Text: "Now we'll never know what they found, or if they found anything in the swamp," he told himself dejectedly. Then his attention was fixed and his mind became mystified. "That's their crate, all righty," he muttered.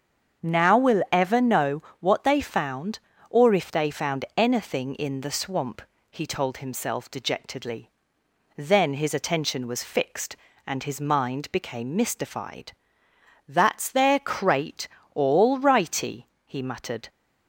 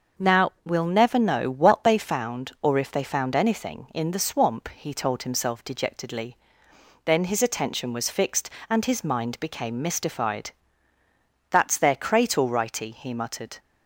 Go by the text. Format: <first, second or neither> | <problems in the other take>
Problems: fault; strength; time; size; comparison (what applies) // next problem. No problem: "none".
second | starts louder than the rest; until 1.5 s; 7 dB; also in the second // says "ever" for "never"; at 1.1 s // pauses between "know" and "what"; slight; at 1.8 s; 0.18 s long